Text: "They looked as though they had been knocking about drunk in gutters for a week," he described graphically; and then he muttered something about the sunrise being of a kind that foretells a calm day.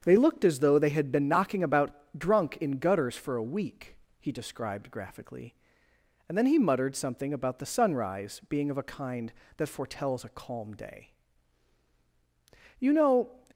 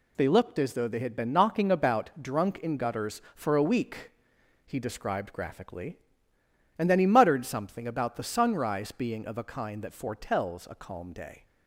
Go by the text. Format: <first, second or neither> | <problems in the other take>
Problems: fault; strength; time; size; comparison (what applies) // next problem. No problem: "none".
second | starts louder than the rest; strong; until 1.0 s; 7 dB // pauses between "about" and "drunk"; slight; at 1.9 s; 0.22 s long // goes on to say "You know"; from 12.8 s on; 0.58 s long